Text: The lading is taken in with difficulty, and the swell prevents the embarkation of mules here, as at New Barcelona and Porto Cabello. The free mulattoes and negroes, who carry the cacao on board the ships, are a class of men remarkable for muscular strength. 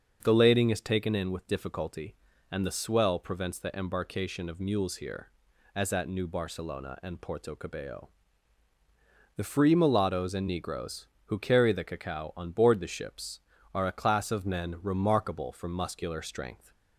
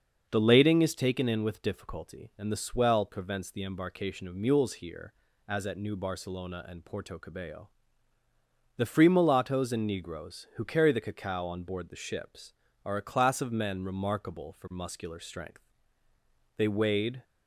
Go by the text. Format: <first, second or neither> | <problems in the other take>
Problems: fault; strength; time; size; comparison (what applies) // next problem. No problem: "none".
first | starts louder than the rest; until 1.3 s; 6.5 dB; also in the first // goes on to say "They wade"; noticeable; from 16.5 s on; 0.68 s long